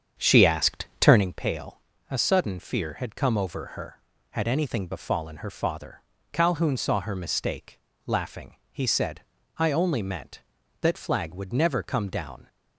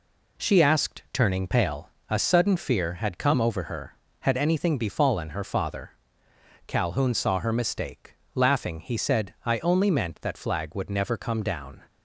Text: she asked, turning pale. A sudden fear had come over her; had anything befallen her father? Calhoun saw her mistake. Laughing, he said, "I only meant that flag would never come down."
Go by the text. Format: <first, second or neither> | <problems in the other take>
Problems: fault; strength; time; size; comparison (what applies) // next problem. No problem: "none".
second | starts louder than the rest; strong; until 1.3 s; 7.5 dB